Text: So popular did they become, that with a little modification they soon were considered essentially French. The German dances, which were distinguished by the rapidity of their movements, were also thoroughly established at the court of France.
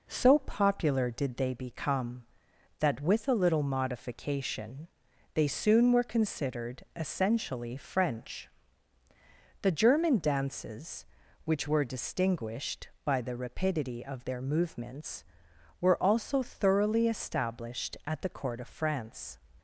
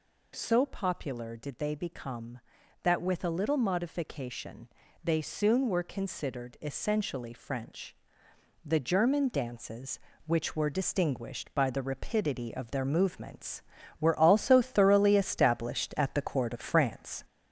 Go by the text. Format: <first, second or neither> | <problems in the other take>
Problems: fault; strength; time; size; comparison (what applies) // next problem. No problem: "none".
first | gets louder; throughout; 3.5 dB // pauses between "modification" and "they"; at 4.6 s; 0.38 s long; noticeable in the first